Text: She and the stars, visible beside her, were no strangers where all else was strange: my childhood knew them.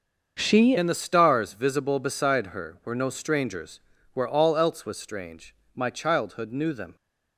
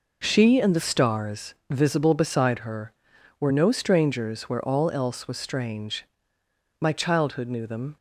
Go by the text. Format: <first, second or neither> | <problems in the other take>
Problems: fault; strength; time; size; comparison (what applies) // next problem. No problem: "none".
second | starts louder than the rest; until 1.4 s; 6.5 dB // changes voice at "and"; from 0.7 s on; 6.2 s long // pauses between "strangers" and "where"; slight; at 3.7 s; 0.34 s long